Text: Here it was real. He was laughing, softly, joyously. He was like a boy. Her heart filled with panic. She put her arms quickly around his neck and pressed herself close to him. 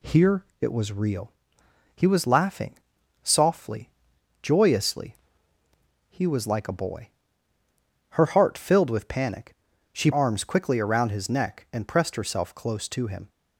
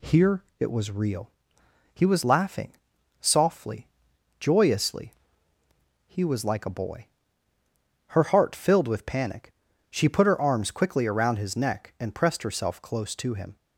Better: second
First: pauses between "Here" and "it"; slight; at 0.4 s; 0.16 s long // skips "put her"; at 10.1 s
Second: pauses between "Here" and "it"; slight; at 0.4 s; 0.16 s long

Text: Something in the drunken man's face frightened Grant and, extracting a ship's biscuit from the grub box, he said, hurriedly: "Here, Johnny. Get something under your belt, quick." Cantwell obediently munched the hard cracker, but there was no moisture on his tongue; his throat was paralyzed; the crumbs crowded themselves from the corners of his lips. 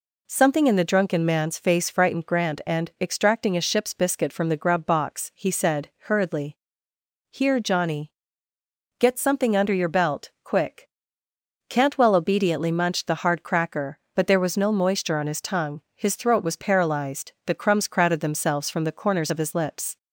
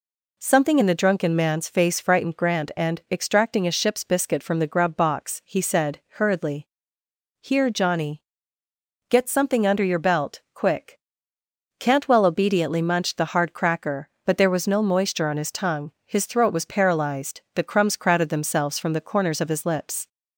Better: neither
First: none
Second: none

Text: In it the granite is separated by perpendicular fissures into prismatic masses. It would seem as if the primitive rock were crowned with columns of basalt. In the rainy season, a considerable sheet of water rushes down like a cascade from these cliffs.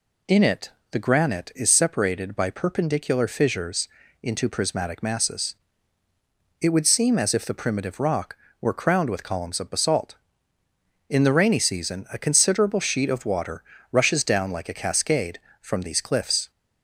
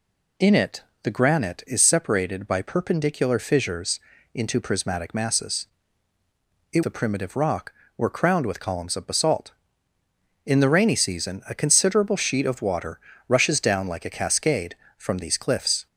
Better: first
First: pauses between "it" and "the"; slight; at 0.7 s; 0.20 s long // pauses between "fissures" and "into"; slight; at 3.8 s; 0.32 s long // pauses between "water" and "rushes"; slight; at 13.6 s; 0.28 s long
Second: pauses between "it" and "the"; slight; at 0.8 s; 0.20 s long // pauses between "fissures" and "into"; slight; at 4.0 s; 0.32 s long // skips "would seem as if"; at 6.8 s // pauses between "water" and "rushes"; slight; at 12.9 s; 0.28 s long

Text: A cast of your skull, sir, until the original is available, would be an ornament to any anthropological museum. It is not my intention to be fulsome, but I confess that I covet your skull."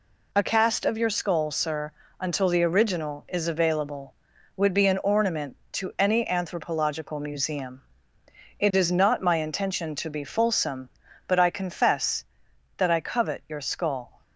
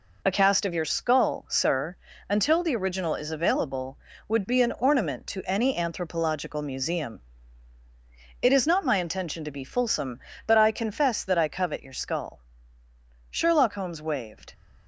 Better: first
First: none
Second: goes on to say "Sherlock Holmes waved"; noticeable; from 13.3 s on; 1.2 s long

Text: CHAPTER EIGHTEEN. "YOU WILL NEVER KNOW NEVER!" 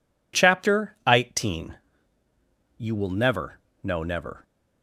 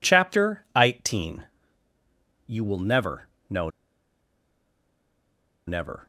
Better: first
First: pauses between "NEVER" and "KNOW"; slight; at 3.6 s; 0.22 s long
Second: pauses between "NEVER" and "KNOW"; slight; at 3.2 s; 0.20 s long // pauses between "KNOW" and "NEVER"; strong; at 3.6 s; 1.9 s long

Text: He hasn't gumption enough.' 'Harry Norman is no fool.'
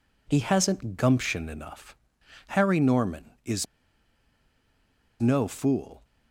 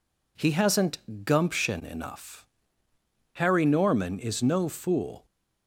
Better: second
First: pauses between "is" and "no"; strong; at 3.6 s; 1.5 s long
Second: none

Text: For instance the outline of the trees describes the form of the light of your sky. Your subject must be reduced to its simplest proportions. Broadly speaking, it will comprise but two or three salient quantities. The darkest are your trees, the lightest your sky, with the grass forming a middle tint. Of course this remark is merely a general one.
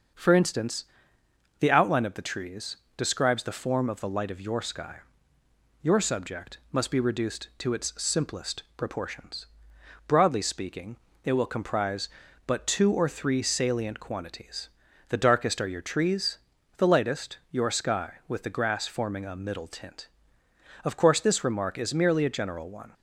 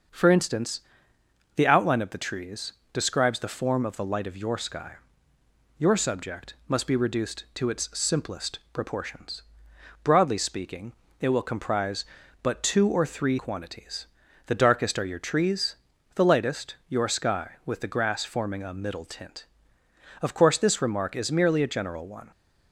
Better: first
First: starts louder than the rest; until 1.9 s; 6.5 dB // pauses between "instance" and "the"; noticeable; at 0.8 s; 0.76 s long // pauses between "trees" and "describes"; slight; at 2.7 s; 0.20 s long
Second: starts louder than the rest; until 1.8 s; 6.5 dB // pauses between "instance" and "the"; noticeable; at 0.8 s; 0.76 s long // pauses between "trees" and "describes"; slight; at 2.7 s; 0.20 s long // skips "salient"; at 13.3 s

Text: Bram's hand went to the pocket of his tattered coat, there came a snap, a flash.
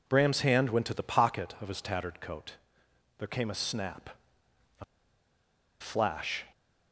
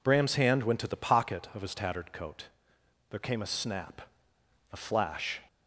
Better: second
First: pauses between "a" and "flash"; noticeable; at 4.8 s; 0.96 s long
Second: none

